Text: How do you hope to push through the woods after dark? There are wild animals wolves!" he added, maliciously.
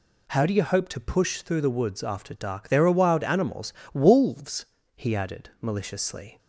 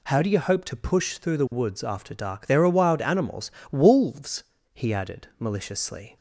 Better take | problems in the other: neither | pauses between "animals" and "wolves"; slight; the same in both

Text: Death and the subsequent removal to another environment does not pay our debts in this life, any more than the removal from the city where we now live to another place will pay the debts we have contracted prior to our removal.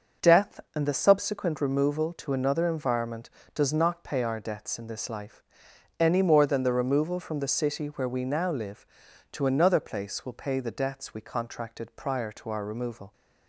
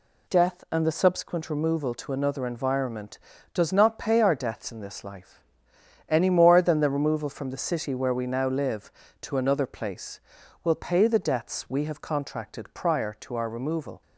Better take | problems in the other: second | skips "have"; at 11.2 s

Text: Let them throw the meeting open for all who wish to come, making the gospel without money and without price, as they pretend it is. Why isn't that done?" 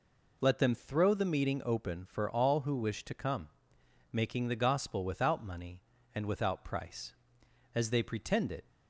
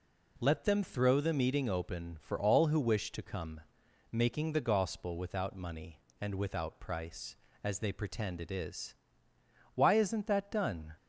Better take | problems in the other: second | stops before "is Why isn't that done"; at 8.6 s

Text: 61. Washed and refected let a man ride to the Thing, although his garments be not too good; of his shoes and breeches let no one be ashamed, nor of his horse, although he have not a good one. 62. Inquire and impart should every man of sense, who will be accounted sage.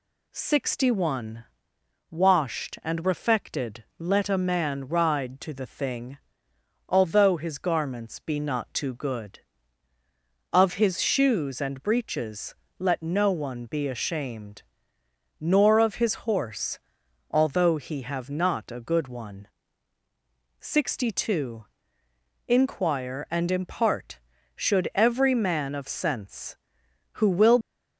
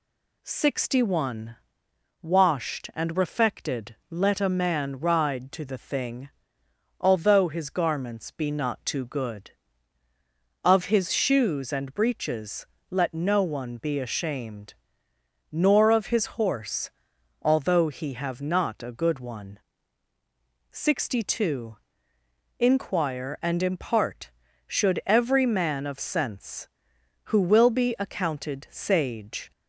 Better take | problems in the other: second | pauses between "breeches" and "let"; slight; at 12.5 s; 0.24 s long; slight in the second // stops before "be accounted sage"; at 27.6 s

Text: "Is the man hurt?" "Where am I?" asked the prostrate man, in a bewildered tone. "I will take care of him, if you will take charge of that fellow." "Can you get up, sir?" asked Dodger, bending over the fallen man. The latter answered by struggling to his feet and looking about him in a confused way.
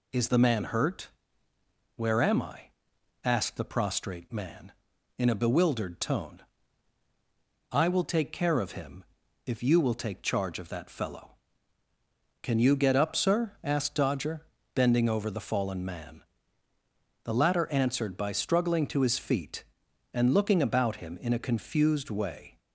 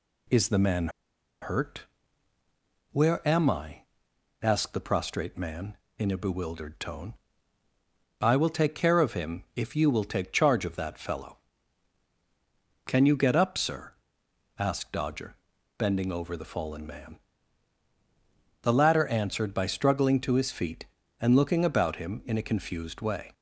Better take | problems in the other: first | pauses between "man" and "hurt"; noticeable; at 0.8 s; 0.53 s long

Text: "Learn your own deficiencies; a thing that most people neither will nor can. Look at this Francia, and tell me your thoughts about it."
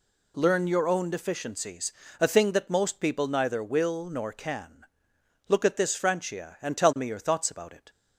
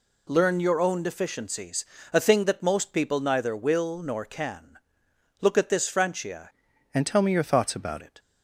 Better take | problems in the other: first | changes voice from "and" to "about"; from 6.9 to 8.0 s; 1.1 s long

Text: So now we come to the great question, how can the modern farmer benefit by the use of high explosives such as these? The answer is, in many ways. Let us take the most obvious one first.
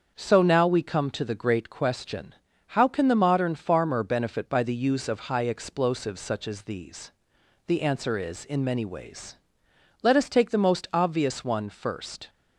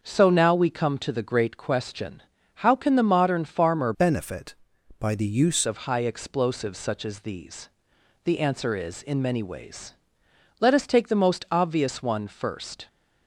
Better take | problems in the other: first | starts louder than the rest; until 1.0 s; 6.5 dB; also in the first // changes voice from "benefit" to "use"; from 3.9 to 5.6 s; 1.7 s long

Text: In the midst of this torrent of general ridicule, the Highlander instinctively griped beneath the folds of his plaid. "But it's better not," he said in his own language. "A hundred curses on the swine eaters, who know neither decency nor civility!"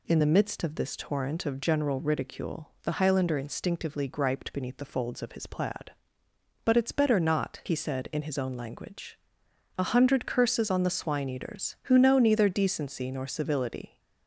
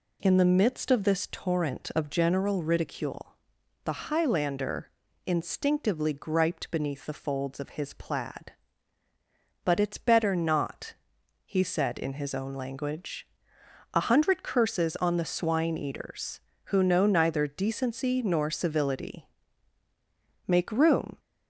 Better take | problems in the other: first | pauses between "Highlander" and "instinctively"; slight; at 4.9 s; 0.34 s long // goes on to say "Make room"; noticeable; from 20.4 s on; 0.74 s long

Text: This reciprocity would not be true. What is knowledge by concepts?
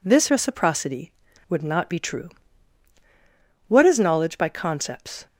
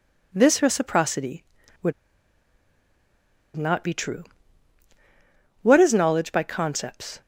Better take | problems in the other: first | pauses between "would" and "not"; strong; at 1.9 s; 1.6 s long

